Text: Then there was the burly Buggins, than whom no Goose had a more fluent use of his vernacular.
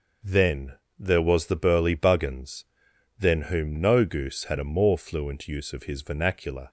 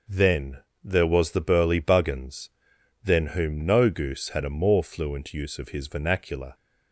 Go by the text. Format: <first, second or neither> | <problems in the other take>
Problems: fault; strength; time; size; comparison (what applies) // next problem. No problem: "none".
neither | pauses between "Then" and "there"; slight; the same in both